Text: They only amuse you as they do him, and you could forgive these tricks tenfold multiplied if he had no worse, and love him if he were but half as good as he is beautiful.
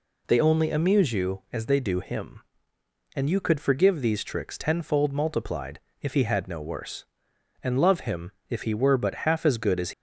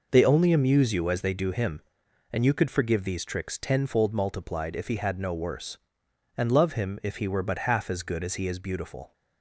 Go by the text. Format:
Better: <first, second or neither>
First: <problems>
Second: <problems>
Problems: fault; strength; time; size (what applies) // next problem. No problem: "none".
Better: second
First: pauses between "multiplied" and "if"; slight; at 5.8 s; 0.20 s long // pauses between "him" and "if"; slight; at 8.3 s; 0.18 s long // stops before "he is beautiful"; at 9.9 s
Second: none